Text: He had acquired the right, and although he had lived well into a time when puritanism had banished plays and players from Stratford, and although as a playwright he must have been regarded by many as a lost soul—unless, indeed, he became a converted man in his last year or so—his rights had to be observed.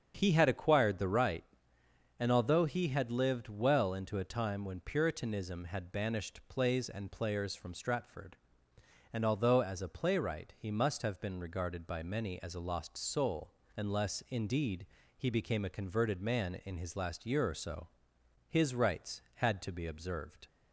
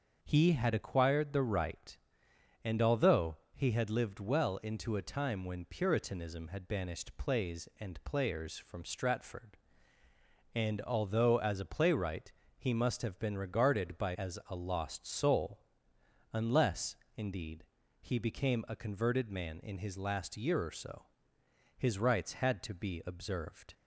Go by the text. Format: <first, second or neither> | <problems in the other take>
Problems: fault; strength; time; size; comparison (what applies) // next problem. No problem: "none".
first | starts louder than the rest; until 1.2 s; 6.5 dB; strong in the first // pauses between "although" and "he"; slight; at 3.3 s; 0.16 s long // pauses between "playwright" and "he"; slight; at 12.3 s; 0.26 s long // skips "many"; at 14.1 s